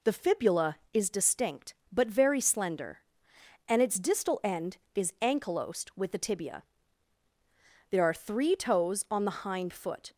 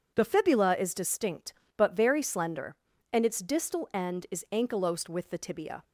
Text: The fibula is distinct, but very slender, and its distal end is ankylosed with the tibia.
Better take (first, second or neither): second